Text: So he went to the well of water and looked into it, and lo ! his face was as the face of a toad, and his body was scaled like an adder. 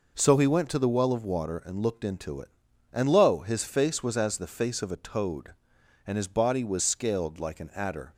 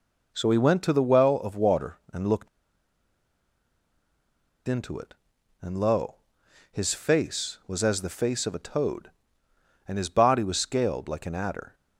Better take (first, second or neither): first